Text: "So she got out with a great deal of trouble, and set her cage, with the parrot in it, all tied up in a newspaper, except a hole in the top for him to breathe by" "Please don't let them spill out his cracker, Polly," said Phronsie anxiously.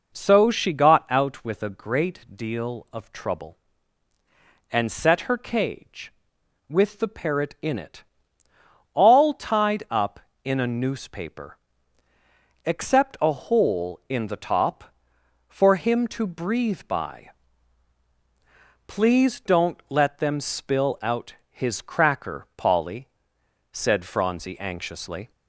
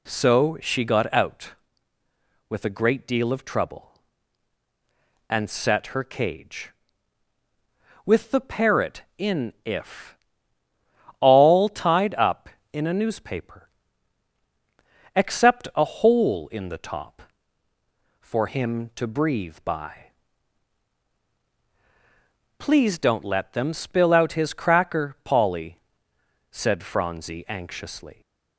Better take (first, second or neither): first